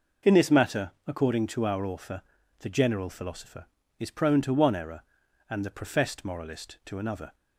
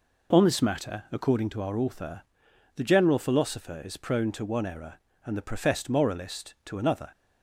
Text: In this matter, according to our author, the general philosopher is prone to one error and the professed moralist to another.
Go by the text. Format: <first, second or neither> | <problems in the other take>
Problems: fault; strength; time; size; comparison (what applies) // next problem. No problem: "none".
first | says "On" for "In"; at 0.3 s